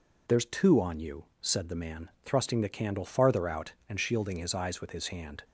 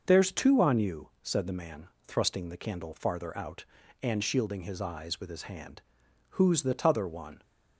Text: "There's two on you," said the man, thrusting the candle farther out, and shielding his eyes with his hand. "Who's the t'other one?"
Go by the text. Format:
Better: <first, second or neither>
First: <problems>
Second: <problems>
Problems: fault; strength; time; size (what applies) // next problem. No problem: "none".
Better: second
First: stops before "Who's the t'other one"; at 5.4 s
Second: none